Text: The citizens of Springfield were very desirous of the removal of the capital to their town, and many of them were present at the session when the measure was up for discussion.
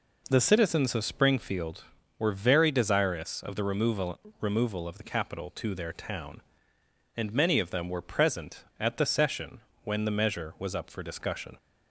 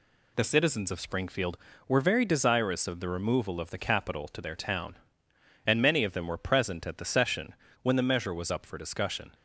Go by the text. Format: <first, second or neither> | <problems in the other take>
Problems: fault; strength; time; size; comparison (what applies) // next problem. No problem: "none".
second | says "removal" twice; at 4.3 s // pauses between "session" and "when"; slight; at 9.6 s; 0.24 s long; slight in the second